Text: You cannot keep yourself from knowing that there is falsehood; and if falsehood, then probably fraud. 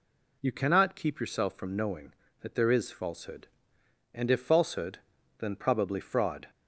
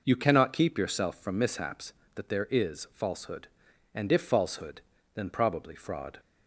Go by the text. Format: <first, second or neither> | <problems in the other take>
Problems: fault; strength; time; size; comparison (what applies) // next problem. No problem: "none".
first | says "mishaps" for "knowing"; at 1.3 s